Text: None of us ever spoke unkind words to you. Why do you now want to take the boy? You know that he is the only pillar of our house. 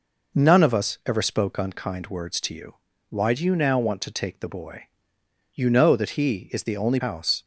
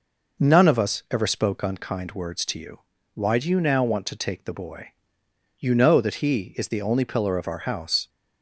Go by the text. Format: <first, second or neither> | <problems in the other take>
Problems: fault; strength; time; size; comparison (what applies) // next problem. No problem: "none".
second | skips "pillar of our"; at 7.0 s